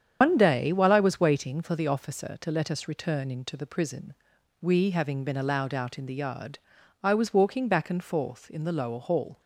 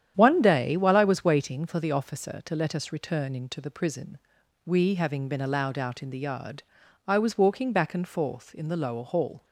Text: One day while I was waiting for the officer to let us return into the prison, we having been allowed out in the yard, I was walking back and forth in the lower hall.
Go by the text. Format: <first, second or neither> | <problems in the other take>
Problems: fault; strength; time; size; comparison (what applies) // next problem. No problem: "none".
second | loses the start of "One"; at 0.2 s; 85 ms // starts louder than the rest; strong; until 1.2 s; 8 dB; strong in the second